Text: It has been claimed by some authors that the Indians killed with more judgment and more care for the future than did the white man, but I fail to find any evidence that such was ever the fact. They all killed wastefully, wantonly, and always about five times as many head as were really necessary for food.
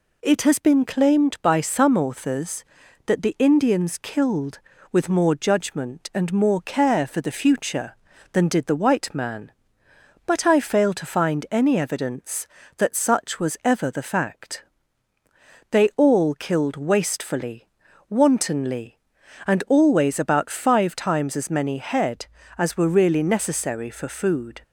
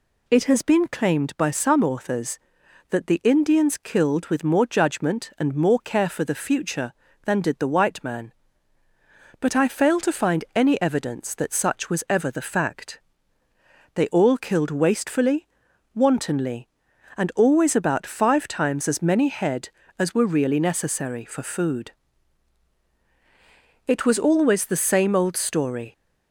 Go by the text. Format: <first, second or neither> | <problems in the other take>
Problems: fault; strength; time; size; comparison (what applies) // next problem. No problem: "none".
first | goes on to say "It was always the same old story"; strong; from 23.8 s on; 2.0 s long